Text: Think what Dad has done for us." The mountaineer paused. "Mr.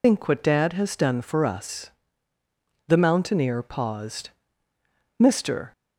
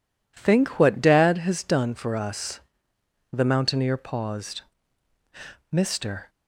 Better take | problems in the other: second | loses the start of "Think"; at 0.0 s; 105 ms

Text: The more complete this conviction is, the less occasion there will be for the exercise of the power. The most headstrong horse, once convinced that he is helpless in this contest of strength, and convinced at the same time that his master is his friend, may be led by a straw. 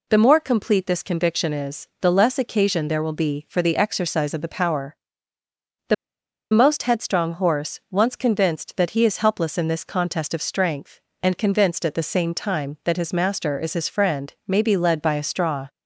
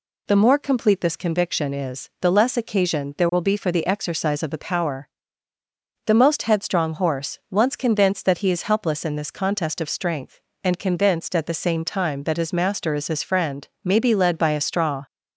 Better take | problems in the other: second | pauses between "The" and "most"; noticeable; at 5.9 s; 0.56 s long

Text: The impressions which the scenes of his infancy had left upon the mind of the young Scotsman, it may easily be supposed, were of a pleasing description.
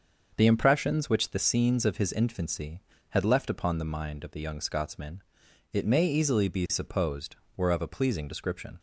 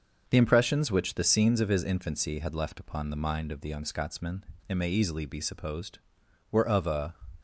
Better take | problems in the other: first | starts louder than the rest; until 1.2 s; 6.5 dB; also in the first // stops before "pleasing description"; at 7.3 s

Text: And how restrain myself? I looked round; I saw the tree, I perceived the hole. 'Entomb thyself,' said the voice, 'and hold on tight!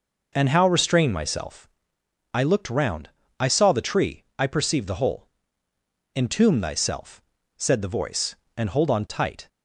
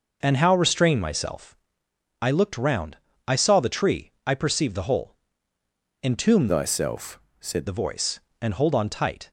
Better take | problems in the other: first | changes voice from "thyself" to "said"; from 6.4 to 7.6 s; 1.2 s long

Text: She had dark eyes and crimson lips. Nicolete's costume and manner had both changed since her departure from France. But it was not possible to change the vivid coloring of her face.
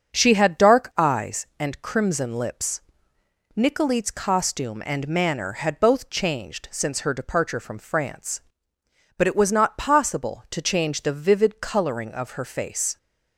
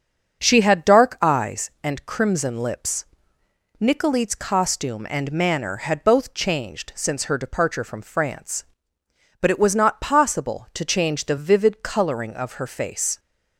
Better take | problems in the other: neither | starts louder than the rest; the same in both

